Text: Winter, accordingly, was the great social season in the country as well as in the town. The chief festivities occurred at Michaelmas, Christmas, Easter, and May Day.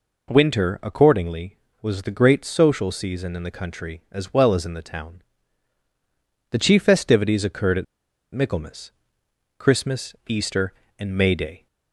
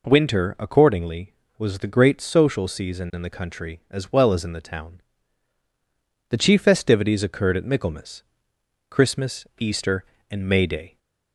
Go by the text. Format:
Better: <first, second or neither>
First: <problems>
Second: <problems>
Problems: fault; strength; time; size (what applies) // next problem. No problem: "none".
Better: second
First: pauses between "at" and "Michaelmas"; noticeable; at 7.8 s; 0.49 s long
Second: none